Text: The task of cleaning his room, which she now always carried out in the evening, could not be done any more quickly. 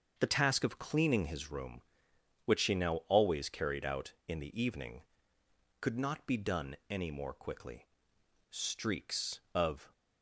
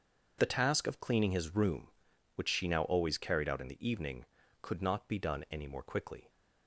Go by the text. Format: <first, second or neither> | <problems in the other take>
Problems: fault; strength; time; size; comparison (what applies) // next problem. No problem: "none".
second | starts louder than the rest; until 1.1 s; 6.5 dB // goes on to say "Streaks of"; from 8.5 s on; 1.4 s long